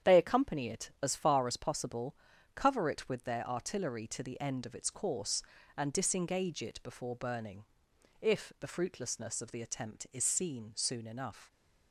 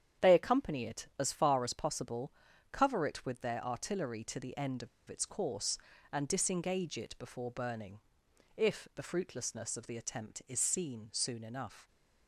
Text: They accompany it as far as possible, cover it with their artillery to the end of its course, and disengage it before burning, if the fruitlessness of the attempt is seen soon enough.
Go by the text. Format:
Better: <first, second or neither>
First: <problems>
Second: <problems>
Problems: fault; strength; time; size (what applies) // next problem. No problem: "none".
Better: first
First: starts louder than the rest; strong; until 1.1 s; 9 dB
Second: starts louder than the rest; strong; until 1.3 s; 9 dB // pauses between "of" and "its"; slight; at 4.8 s; 0.21 s long